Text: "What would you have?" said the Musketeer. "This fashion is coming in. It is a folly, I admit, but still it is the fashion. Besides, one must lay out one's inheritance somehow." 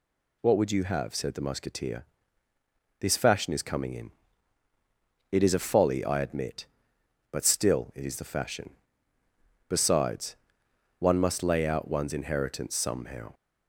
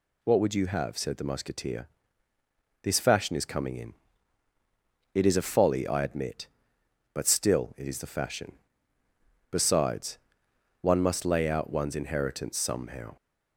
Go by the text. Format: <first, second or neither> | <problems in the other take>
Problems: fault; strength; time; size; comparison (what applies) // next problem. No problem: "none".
neither | none